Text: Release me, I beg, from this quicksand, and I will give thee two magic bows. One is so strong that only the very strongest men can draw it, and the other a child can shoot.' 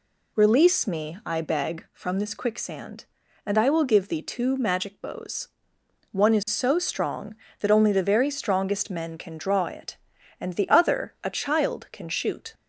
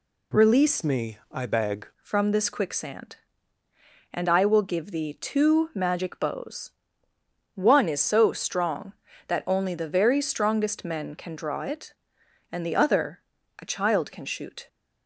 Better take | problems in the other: first | changes voice from "me" to "beg"; from 0.8 to 1.8 s; 1.0 s long // pauses between "other" and "a"; slight; at 13.2 s; 0.36 s long

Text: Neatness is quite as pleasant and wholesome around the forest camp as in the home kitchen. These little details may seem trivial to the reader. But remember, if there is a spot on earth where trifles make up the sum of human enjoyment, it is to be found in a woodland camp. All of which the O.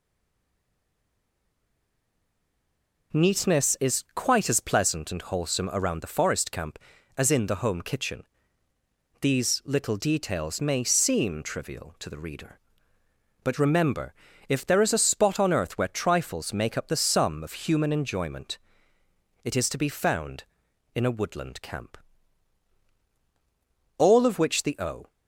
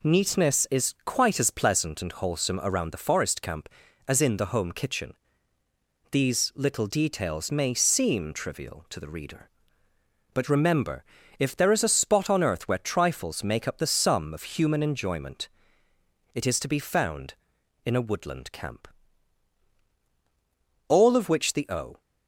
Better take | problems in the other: second | stays silent before the first word; strong; until 3.1 s; 3.1 s long

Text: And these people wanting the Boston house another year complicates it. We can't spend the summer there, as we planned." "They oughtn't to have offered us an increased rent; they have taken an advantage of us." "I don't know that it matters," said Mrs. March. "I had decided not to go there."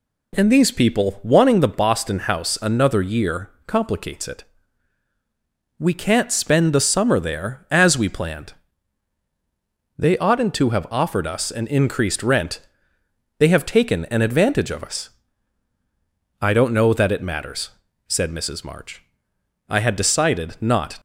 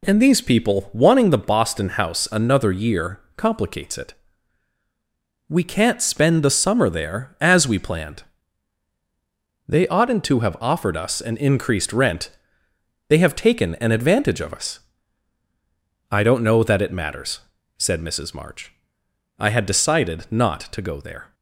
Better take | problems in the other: second | pauses between "year" and "complicates"; slight; at 3.4 s; 0.16 s long; slight in the second // stops before "to go there"; at 20.9 s

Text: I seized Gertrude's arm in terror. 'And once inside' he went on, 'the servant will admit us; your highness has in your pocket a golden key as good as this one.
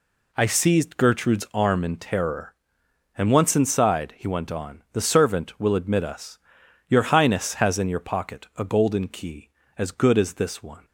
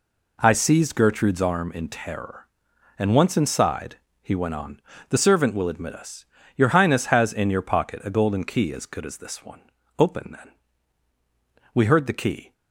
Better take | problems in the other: first | pauses between "inside" and "he"; slight; at 3.9 s; 0.24 s long // goes on to say "Open then We heard the key"; strong; from 9.9 s on; 2.5 s long

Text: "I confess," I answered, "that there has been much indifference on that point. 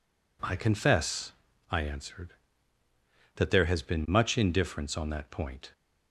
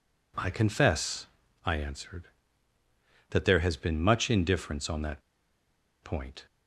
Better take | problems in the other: first | pauses between "that" and "point"; noticeable; at 5.2 s; 0.82 s long

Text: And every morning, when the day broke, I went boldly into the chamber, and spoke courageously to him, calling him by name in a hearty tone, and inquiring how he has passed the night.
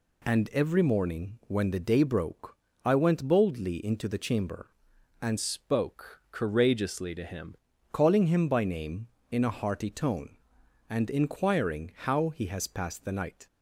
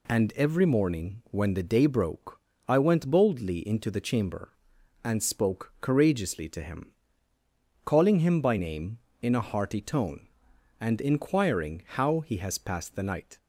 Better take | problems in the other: second | changes voice from "spoke" to "him"; from 5.3 to 7.5 s; 2.2 s long

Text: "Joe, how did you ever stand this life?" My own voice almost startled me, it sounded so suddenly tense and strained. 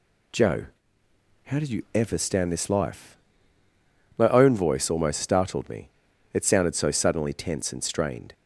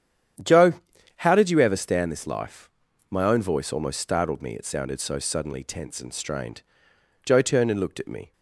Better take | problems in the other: first | starts louder than the rest; strong; until 1.8 s; 9.5 dB // goes on to say "Joe turned and looked at me"; noticeable; from 7.2 s on; 1.0 s long

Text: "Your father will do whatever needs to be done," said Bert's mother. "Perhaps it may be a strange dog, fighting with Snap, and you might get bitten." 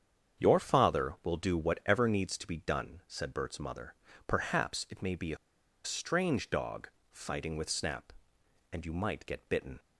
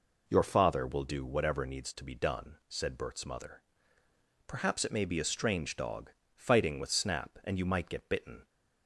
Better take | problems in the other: second | starts louder than the rest; strong; until 1.4 s; 7.5 dB // pauses between "a" and "strange"; noticeable; at 5.3 s; 0.47 s long

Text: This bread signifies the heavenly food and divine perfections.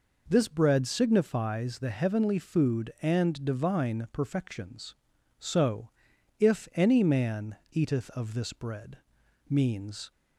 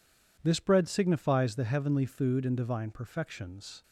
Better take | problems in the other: second | goes on to say "So If any man eateth of this bread means"; strong; from 5.3 s on; 4.7 s long

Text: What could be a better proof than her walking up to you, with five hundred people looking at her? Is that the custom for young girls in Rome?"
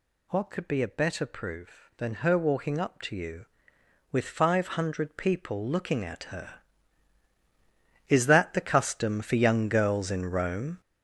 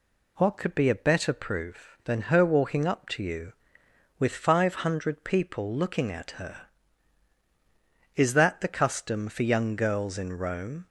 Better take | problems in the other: second | gets louder; strong; throughout; 8 dB

